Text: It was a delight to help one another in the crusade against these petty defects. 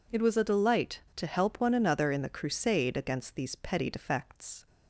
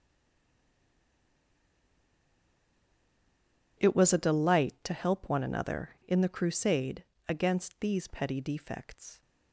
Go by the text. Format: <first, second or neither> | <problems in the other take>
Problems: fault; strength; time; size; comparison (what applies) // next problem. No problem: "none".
first | stays silent before the first word; strong; until 3.7 s; 3.7 s long // pauses between "crusade" and "against"; slight; at 7.0 s; 0.24 s long